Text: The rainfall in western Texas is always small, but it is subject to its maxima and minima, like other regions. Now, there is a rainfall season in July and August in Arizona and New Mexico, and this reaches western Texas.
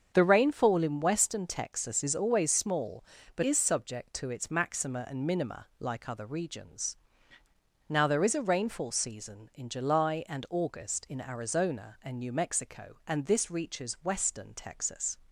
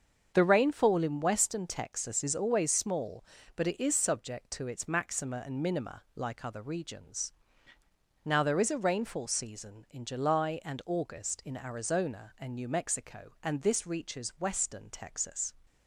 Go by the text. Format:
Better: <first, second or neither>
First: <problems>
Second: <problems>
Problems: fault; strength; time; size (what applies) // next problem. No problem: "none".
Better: second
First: starts louder than the rest; until 1.1 s; 7 dB // skips "it"; at 3.4 s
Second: starts louder than the rest; until 1.3 s; 7 dB